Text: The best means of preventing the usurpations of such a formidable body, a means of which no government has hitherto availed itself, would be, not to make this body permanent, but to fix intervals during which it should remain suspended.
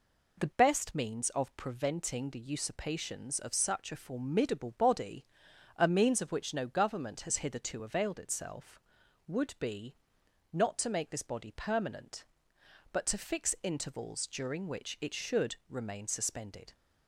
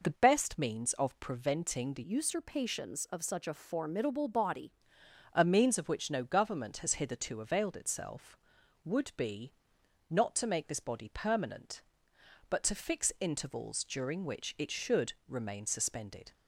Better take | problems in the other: first | changes voice from "usurpations" to "body"; from 2.0 to 4.7 s; 2.7 s long // pauses between "should" and "remain"; slight; at 15.1 s; 0.16 s long

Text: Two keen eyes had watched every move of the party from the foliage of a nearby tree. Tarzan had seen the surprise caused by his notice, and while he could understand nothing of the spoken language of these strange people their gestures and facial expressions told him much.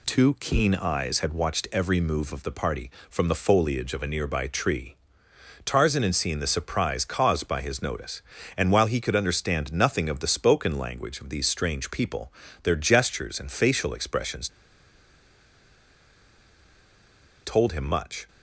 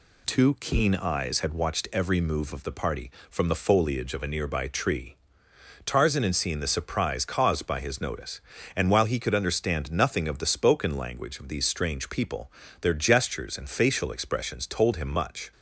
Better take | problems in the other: second | pauses between "people" and "their"; slight; at 12.3 s; 0.30 s long; slight in the second // pauses between "expressions" and "told"; strong; at 14.4 s; 2.9 s long

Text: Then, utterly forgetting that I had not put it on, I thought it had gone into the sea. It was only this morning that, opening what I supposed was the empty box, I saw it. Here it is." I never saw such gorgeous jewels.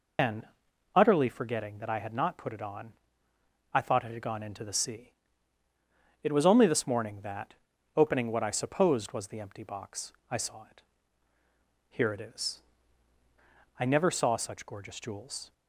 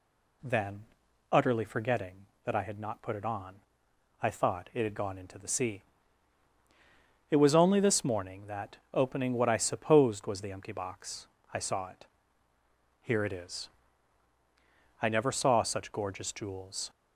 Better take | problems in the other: second | loses the start of "Then"; at 0.1 s; 145 ms

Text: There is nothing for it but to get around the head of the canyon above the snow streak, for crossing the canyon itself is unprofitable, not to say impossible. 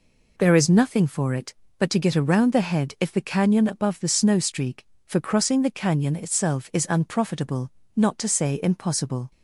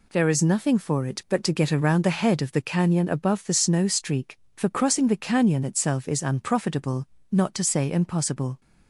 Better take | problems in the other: second | says "if" for "of"; at 3.0 s

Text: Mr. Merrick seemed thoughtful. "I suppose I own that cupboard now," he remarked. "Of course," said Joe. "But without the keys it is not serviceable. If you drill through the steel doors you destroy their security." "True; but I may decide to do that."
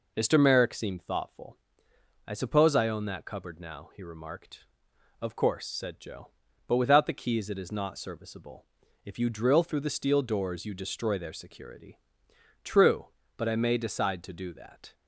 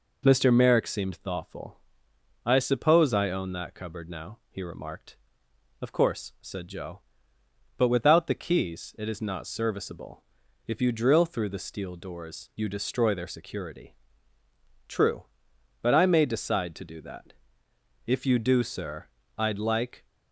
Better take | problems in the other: first | goes on to say "If you do sir I'd like"; strong; from 18.0 s on; 2.0 s long

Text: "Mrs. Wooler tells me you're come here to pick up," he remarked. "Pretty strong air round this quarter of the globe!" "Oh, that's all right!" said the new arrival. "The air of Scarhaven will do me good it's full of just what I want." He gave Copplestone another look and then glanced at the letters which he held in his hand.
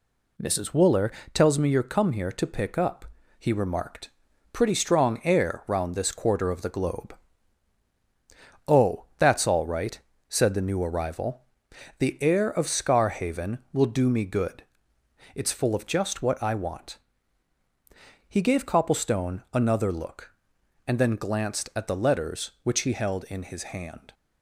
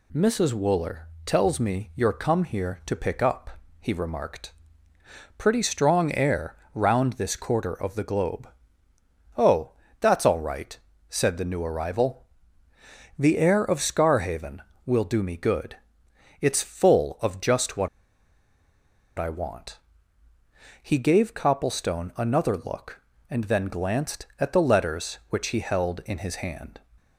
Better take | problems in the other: first | pauses between "Wooler" and "tells"; slight; at 1.0 s; 0.20 s long; slight in the first // pauses between "air" and "round"; slight; at 6.5 s; 0.18 s long // pauses between "good" and "it's"; noticeable; at 15.7 s; 0.64 s long; noticeable in the first // pauses between "what" and "I"; strong; at 17.8 s; 1.3 s long

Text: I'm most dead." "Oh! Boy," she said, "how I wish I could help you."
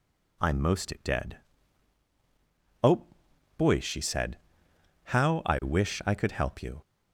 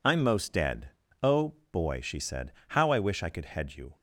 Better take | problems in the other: first | says "head" for "help"; at 3.4 s

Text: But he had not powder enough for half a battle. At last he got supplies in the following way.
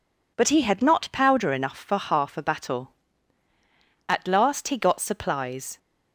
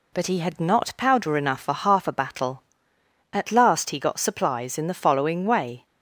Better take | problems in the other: second | stops before "in the following way"; at 5.7 s

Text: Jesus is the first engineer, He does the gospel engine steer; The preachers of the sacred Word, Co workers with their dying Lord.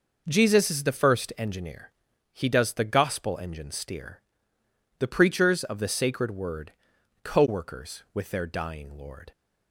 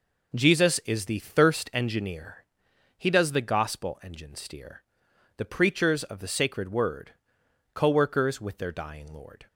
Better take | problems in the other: first | starts louder than the rest; noticeable; until 1.4 s; 6 dB // says "thirst" for "first"; at 1.1 s

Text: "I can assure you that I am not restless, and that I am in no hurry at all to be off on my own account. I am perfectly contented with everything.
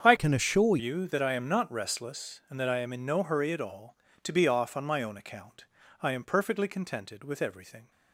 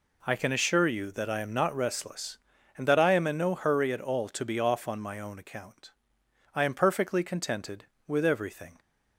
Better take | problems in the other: second | starts louder than the rest; strong; until 1.0 s; 7.5 dB // changes voice from "can" to "assure"; from 0.1 to 0.7 s; 0.6 s long

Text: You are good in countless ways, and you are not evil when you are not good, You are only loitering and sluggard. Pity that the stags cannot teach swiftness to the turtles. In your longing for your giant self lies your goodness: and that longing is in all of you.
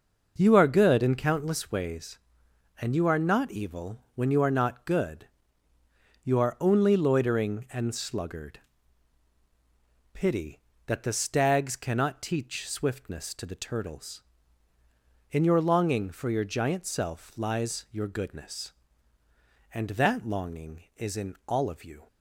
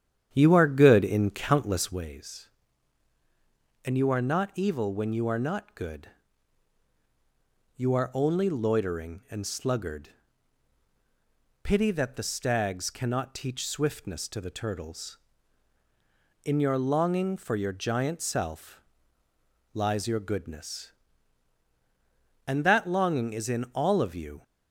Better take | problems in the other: first | starts louder than the rest; strong; until 2.1 s; 9 dB // pauses between "self" and "lies"; noticeable; at 18.8 s; 0.92 s long

